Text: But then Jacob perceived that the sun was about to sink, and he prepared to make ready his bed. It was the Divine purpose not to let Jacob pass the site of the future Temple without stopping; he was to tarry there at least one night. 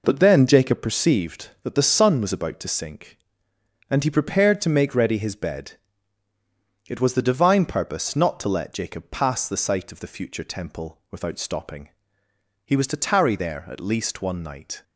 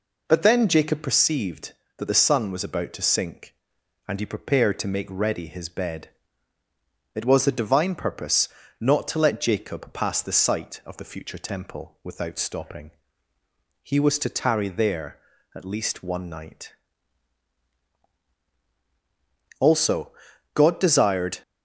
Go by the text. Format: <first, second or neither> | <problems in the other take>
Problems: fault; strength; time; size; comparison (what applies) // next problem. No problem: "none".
first | pauses between "purpose" and "not"; slight; at 8.4 s; 0.32 s long // goes on to say "Also God desired"; strong; from 19.5 s on; 1.8 s long